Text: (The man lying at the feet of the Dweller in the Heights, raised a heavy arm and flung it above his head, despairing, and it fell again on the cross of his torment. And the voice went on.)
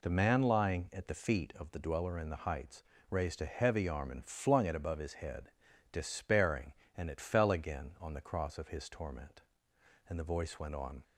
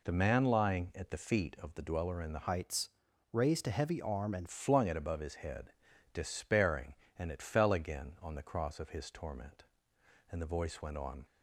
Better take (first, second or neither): first